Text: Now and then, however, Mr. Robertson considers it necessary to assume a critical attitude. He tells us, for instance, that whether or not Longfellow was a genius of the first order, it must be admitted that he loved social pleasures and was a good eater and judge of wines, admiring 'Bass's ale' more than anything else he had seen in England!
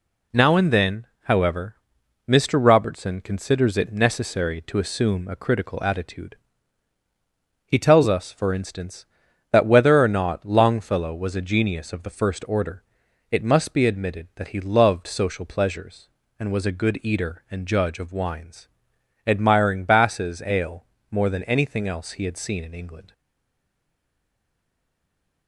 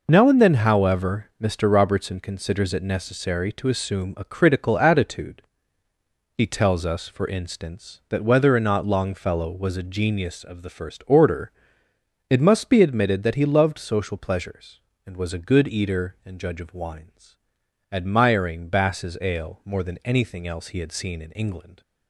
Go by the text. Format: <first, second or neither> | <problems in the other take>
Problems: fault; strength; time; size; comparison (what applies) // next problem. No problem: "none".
second | pauses between "ale" and "more"; slight; at 20.8 s; 0.26 s long // stays silent after the last word; from 23.1 s on; 2.3 s long